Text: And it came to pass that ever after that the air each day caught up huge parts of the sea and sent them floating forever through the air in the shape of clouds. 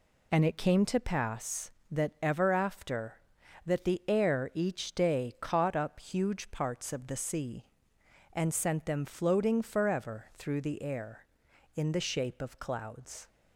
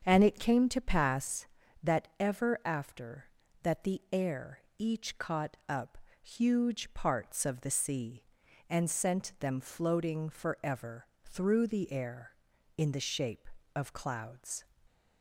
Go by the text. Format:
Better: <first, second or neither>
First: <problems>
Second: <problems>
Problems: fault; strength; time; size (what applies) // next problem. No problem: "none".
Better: first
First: none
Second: starts louder than the rest; until 1.0 s; 7 dB // pauses between "air" and "each"; slight; at 4.5 s; 0.18 s long // skips "day"; at 5.1 s // pauses between "up" and "huge"; slight; at 5.9 s; 0.24 s long // pauses between "forever" and "through"; slight; at 11.0 s; 0.20 s long